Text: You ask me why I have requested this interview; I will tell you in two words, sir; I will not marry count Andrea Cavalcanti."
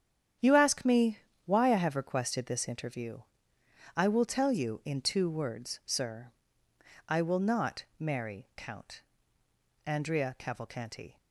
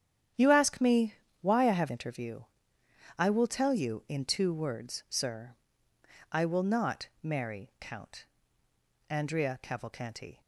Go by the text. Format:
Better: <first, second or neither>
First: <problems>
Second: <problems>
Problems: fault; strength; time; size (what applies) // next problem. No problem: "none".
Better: first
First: starts louder than the rest; strong; until 1.6 s; 9 dB // pauses between "me" and "why"; slight; at 1.1 s; 0.28 s long // pauses between "count" and "Andrea"; noticeable; at 9.0 s; 0.86 s long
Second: starts louder than the rest; strong; until 1.6 s; 9.5 dB // pauses between "me" and "why"; slight; at 1.1 s; 0.28 s long // skips "requested this"; at 1.8 s // pauses between "count" and "Andrea"; noticeable; at 8.2 s; 0.86 s long